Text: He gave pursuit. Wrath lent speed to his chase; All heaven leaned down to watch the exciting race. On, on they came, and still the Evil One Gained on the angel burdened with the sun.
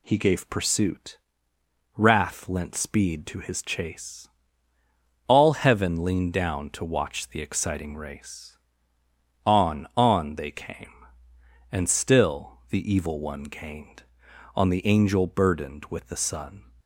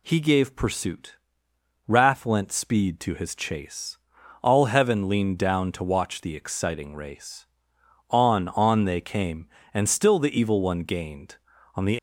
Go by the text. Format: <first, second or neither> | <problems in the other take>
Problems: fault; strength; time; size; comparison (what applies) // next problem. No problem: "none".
first | stops before "angel burdened with the sun"; at 11.9 s